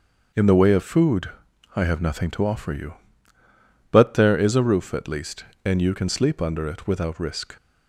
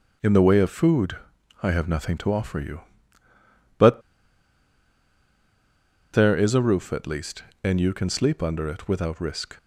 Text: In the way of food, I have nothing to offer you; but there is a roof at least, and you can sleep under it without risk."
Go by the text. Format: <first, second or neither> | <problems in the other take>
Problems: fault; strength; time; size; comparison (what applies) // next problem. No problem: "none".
first | starts louder than the rest; until 1.7 s; 7 dB; also in the first // pauses between "but" and "there"; strong; at 4.0 s; 2.1 s long